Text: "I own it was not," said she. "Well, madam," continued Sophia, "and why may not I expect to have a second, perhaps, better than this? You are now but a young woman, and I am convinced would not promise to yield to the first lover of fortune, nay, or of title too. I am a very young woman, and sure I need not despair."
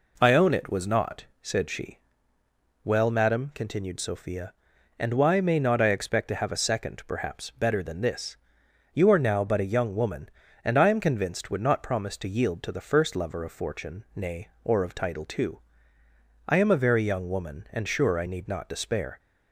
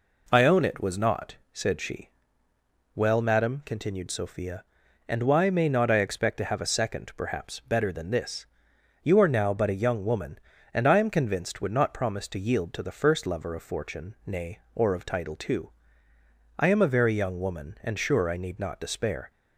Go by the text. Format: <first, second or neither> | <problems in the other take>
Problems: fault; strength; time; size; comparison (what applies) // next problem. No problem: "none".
neither | none